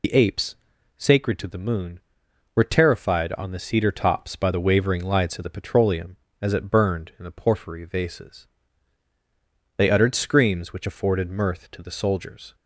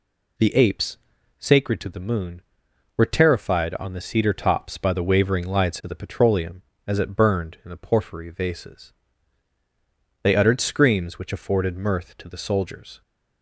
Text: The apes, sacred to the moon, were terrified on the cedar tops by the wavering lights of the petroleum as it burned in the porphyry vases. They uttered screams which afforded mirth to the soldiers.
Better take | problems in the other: second | loses the start of "The"; at 0.0 s; 75 ms

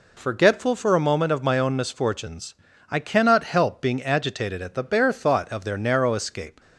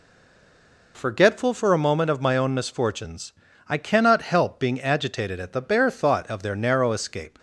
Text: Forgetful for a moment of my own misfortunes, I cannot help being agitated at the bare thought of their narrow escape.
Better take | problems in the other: first | stays silent before the first word; slight; until 0.9 s; 0.9 s long

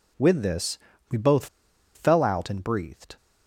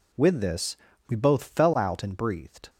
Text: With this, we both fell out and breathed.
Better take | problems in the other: second | pauses between "both" and "fell"; noticeable; at 1.4 s; 0.49 s long

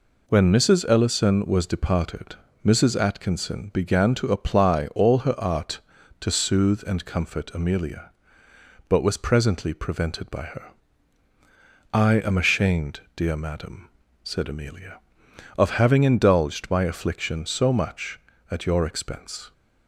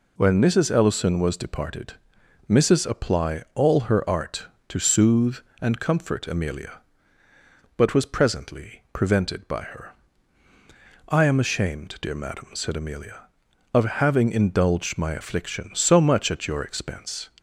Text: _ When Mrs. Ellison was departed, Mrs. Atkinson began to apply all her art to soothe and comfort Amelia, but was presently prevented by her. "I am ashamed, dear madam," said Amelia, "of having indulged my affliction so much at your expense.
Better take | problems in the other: first | skips "Atkinson began to"; at 2.8 s

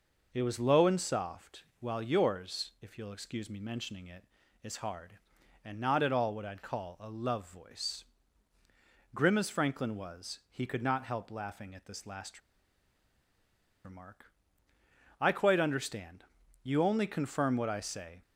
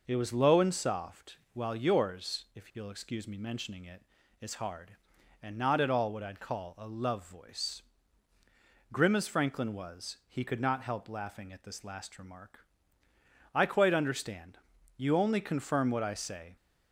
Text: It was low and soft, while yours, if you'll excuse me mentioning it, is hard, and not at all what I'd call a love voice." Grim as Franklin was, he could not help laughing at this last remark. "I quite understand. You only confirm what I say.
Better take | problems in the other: second | pauses between "last" and "remark"; strong; at 12.3 s; 1.4 s long

